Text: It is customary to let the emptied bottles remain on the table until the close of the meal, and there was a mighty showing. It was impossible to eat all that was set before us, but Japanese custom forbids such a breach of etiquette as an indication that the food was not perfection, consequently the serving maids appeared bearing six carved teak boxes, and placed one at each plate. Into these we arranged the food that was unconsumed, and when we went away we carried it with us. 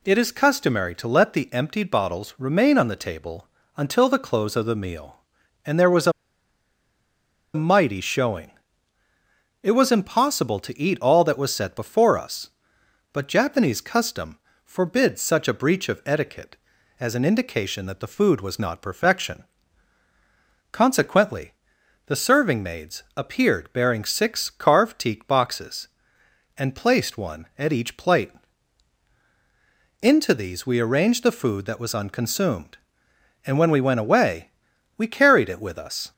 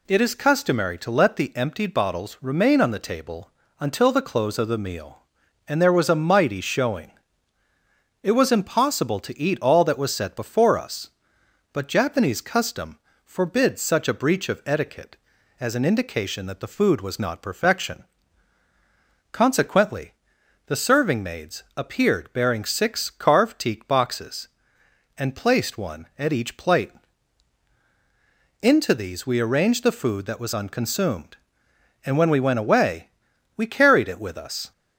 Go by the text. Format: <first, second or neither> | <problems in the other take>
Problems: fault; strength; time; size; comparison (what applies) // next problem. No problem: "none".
second | pauses between "table" and "until"; slight; at 3.4 s; 0.30 s long; slight in the second // pauses between "a" and "mighty"; strong; at 6.1 s; 1.4 s long // pauses between "custom" and "forbids"; slight; at 14.3 s; 0.26 s long; slight in the second // pauses between "consequently" and "the"; noticeable; at 21.5 s; 0.54 s long; noticeable in the second // pauses between "away" and "we"; noticeable; at 34.5 s; 0.48 s long; noticeable in the second